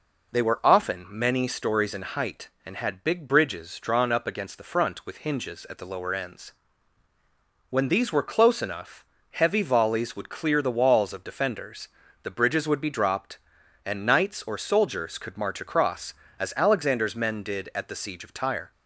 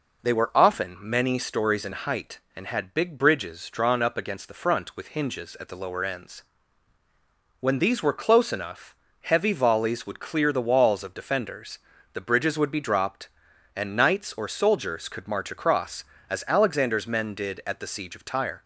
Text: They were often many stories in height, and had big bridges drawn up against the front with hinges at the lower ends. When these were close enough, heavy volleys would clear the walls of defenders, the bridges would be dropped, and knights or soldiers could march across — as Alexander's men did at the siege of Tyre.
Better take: neither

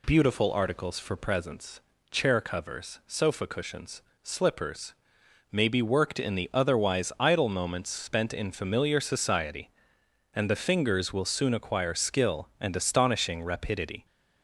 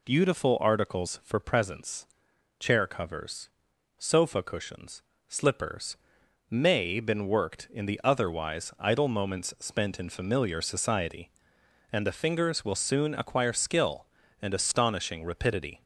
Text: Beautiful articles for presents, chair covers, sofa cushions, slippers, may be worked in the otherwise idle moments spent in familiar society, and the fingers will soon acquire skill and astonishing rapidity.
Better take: first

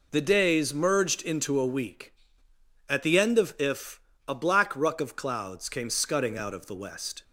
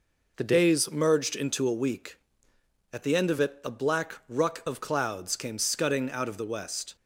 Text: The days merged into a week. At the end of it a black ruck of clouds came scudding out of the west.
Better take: second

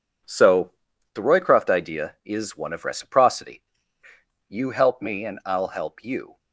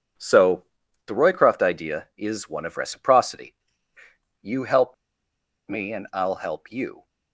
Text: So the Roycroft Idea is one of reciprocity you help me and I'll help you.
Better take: first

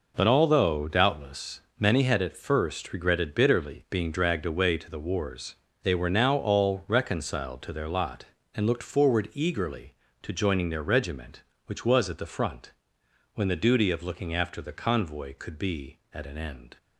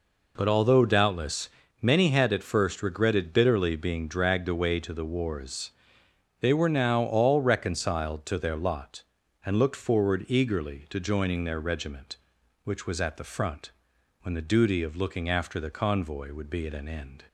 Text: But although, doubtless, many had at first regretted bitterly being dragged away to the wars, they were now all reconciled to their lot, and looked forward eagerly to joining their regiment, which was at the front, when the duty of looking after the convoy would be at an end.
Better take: second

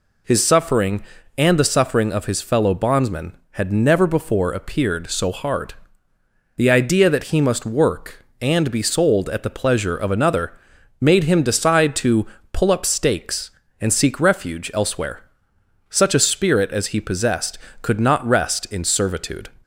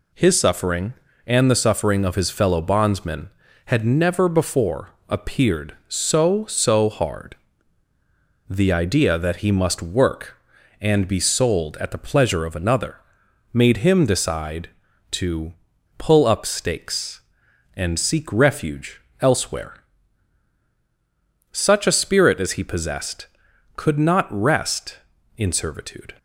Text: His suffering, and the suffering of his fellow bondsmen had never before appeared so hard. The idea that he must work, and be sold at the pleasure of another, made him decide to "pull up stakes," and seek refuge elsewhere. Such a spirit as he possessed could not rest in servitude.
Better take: first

